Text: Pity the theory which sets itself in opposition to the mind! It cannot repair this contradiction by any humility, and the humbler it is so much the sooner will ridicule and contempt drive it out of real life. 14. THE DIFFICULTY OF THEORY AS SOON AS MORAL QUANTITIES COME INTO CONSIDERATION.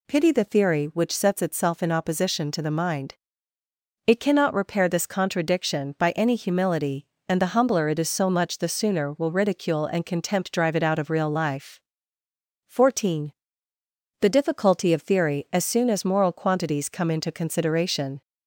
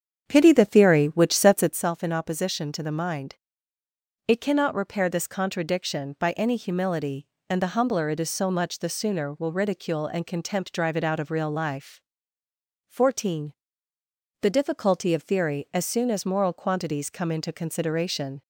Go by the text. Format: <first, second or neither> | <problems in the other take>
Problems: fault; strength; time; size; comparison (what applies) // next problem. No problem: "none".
first | starts louder than the rest; strong; until 1.8 s; 8 dB